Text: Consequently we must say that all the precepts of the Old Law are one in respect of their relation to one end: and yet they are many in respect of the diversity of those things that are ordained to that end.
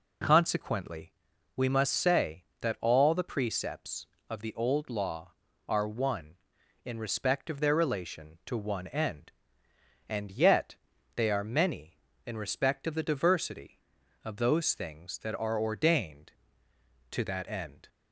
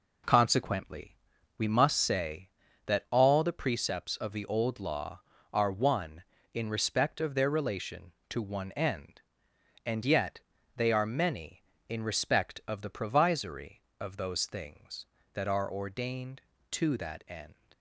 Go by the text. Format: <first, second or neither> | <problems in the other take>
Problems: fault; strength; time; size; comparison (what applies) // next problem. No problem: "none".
first | pauses between "Consequently" and "we"; at 1.1 s; 0.44 s long; also in the first // pauses between "yet" and "they"; at 10.3 s; 0.38 s long; also in the first // says "provisory" for "diversity"; at 12.8 s